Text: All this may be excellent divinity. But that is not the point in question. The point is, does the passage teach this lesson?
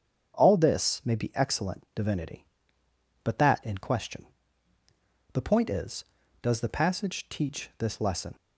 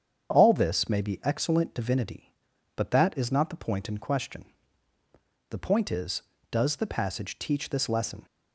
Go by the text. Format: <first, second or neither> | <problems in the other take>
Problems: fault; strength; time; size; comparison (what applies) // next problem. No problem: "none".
second | starts louder than the rest; strong; until 1.4 s; 7.5 dB; strong in the second // skips "is not the point"; at 3.6 s